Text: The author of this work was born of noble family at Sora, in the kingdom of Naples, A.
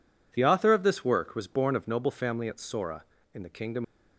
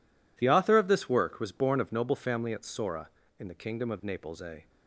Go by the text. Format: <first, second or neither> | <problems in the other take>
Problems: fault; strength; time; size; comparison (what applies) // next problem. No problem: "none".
second | stops before "of Naples A"; at 3.8 s